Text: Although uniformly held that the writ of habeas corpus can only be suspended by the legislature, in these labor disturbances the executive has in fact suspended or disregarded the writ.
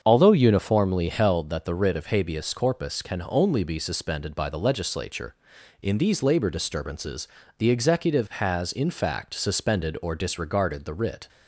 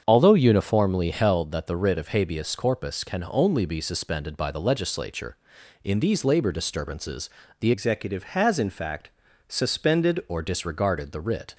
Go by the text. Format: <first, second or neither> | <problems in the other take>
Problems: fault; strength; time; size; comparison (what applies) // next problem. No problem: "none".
first | starts louder than the rest; strong; until 1.0 s; 7.5 dB; strong in the first // pauses between "disturbances" and "the"; slight; at 7.2 s; 0.32 s long; slight in the first // changes voice from "executive" to "suspended"; from 7.7 to 10.2 s; 2.5 s long // pauses between "fact" and "suspended"; at 9.1 s; 0.38 s long